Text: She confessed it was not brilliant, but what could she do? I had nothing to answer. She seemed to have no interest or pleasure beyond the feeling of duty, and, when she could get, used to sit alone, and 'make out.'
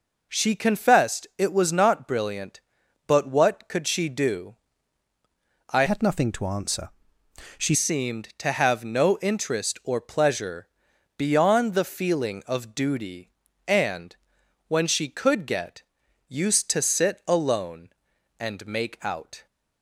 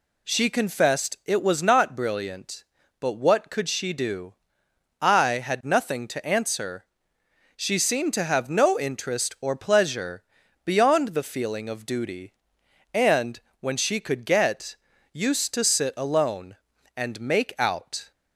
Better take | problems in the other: second | changes voice from "had" to "She"; from 5.8 to 7.7 s; 1.9 s long // pauses between "pleasure" and "beyond"; noticeable; at 10.6 s; 0.48 s long; also in the second

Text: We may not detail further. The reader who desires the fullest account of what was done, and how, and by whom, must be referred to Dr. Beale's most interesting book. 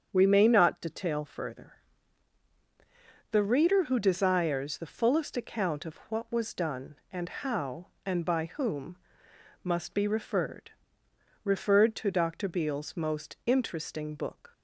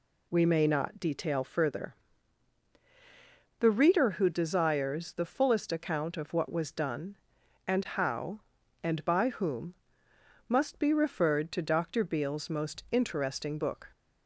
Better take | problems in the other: second | starts louder than the rest; strong; until 1.1 s; 7.5 dB // says "referred" twice; at 11.4 s

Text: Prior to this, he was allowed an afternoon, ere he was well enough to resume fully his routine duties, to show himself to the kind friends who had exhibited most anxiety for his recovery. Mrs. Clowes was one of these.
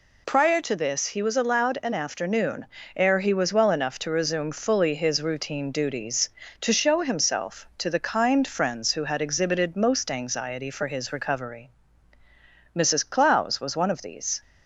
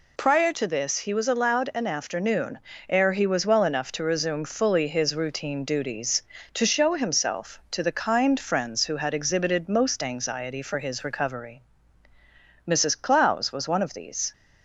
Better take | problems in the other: neither | none

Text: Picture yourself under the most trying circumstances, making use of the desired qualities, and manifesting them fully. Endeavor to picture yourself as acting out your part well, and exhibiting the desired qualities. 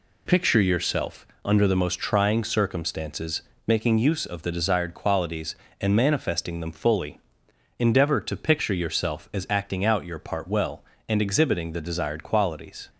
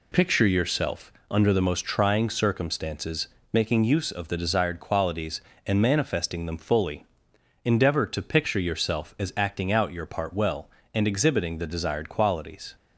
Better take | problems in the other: neither | pauses between "yourself" and "under"; slight; the same in both

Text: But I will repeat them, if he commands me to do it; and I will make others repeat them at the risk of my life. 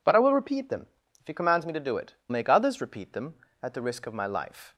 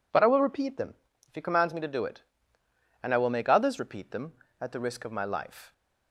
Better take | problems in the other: second | skips "and I will"; at 2.2 s

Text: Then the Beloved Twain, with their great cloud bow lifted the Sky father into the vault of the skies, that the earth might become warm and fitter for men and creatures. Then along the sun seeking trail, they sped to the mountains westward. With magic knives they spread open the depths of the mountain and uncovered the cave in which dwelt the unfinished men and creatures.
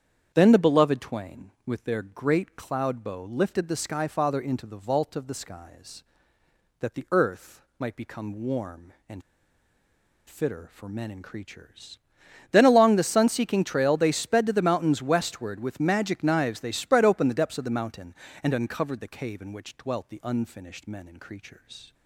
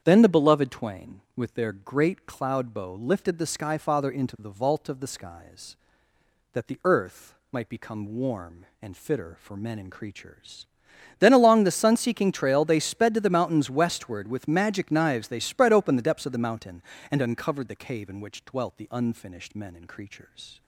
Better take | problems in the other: second | starts louder than the rest; strong; until 1.3 s; 8.5 dB; strong in the second // pauses between "earth" and "might"; slight; at 7.6 s; 0.16 s long; slight in the second // pauses between "and" and "fitter"; at 9.2 s; 1.0 s long

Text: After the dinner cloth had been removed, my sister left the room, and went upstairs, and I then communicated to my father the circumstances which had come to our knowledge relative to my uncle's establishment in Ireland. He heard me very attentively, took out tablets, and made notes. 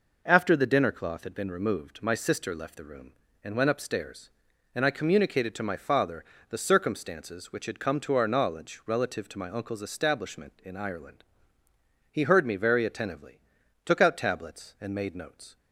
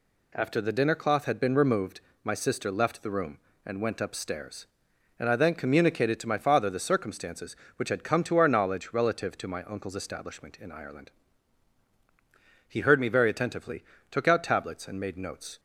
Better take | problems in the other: second | skips "then"; at 4.9 s // pauses between "father" and "the"; slight; at 6.2 s; 0.24 s long

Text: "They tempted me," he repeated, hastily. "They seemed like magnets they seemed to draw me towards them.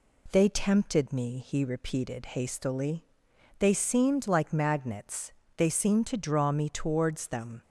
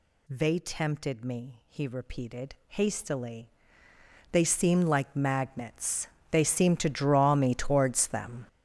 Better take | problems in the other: first | gets louder; strong; throughout; 11 dB // pauses between "magnets" and "they"; slight; at 6.0 s; 0.24 s long; slight in the first

